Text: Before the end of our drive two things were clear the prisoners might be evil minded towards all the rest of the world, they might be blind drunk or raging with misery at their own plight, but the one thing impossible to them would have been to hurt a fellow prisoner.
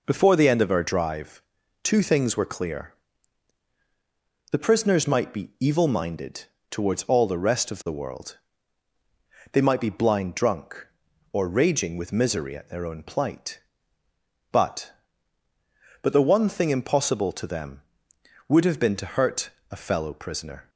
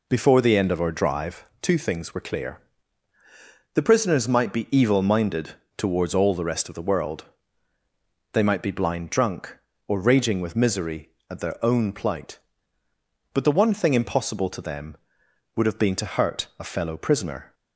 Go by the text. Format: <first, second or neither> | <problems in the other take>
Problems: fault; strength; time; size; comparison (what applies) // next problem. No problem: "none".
second | pauses between "drive" and "two"; at 1.4 s; 0.40 s long; slight in the second // pauses between "clear" and "the"; strong; at 2.9 s; 1.5 s long; also in the second // pauses between "minded" and "towards"; slight; at 6.4 s; 0.26 s long; slight in the second // says "but" twice; at 16.0 s // pauses between "hurt" and "a"; slight; at 19.5 s; 0.18 s long